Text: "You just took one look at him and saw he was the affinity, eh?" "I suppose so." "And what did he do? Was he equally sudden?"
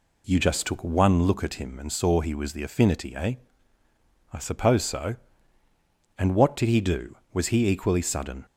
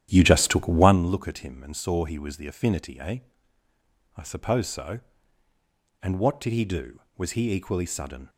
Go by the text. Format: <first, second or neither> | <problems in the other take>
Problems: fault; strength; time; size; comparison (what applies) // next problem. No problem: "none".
first | starts louder than the rest; strong; until 1.0 s; 11 dB